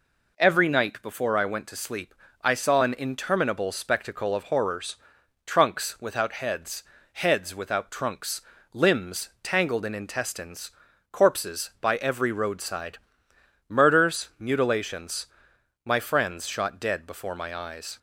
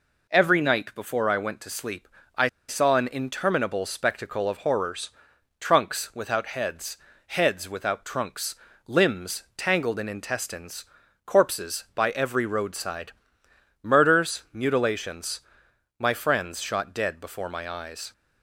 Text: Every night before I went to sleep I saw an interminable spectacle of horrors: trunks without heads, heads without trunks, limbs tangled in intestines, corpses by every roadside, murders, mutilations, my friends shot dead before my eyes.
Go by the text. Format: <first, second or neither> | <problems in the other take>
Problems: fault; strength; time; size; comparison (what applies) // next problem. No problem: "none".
first | pauses between "sleep" and "I"; slight; at 2.0 s; 0.32 s long; slight in the first // pauses between "I" and "saw"; slight; at 2.4 s; 0.19 s long